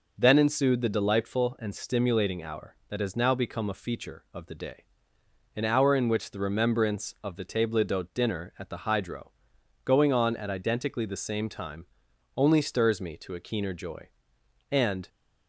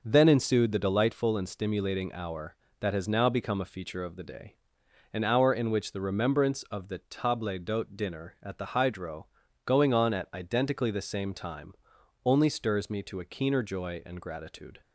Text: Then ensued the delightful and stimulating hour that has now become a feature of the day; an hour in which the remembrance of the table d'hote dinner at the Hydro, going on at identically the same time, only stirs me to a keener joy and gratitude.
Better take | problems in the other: second | stops before "gratitude"; at 15.0 s

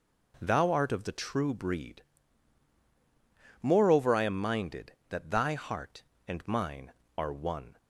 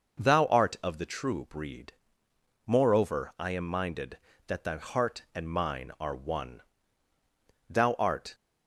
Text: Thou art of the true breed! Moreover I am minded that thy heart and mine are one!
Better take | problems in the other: first | goes on to say "Thou art"; noticeable; from 7.7 s on; 0.64 s long

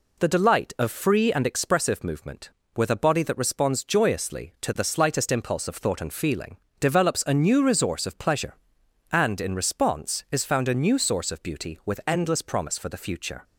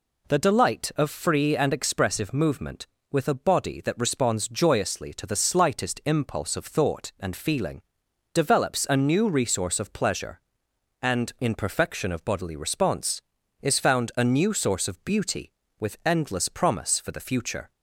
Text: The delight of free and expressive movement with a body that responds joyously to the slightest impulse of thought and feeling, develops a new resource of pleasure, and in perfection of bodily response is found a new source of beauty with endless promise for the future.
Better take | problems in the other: second | skips "perfection of bodily"; at 9.5 s

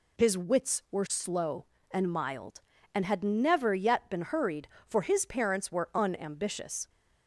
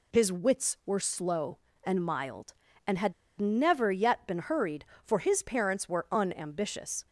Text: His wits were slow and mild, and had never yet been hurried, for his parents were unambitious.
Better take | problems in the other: first | pauses between "had" and "never"; slight; at 3.1 s; 0.26 s long

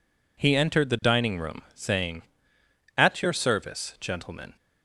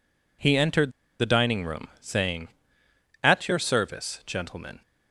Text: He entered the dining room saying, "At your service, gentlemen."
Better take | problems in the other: first | pauses between "entered" and "the"; slight; at 0.8 s; 0.30 s long

